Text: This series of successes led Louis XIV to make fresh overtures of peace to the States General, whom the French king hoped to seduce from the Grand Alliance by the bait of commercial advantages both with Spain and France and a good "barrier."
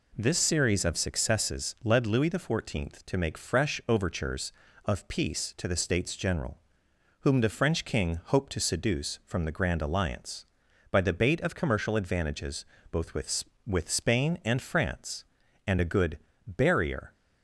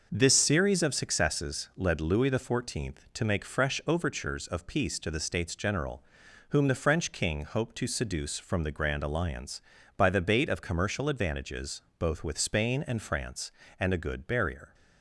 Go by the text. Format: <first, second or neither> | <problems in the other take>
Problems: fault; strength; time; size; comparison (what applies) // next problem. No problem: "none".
second | pauses between "advantages" and "both"; slight; at 12.6 s; 0.28 s long; slight in the second // says "with" twice; at 13.6 s // pauses between "good" and "barrier"; slight; at 16.1 s; 0.28 s long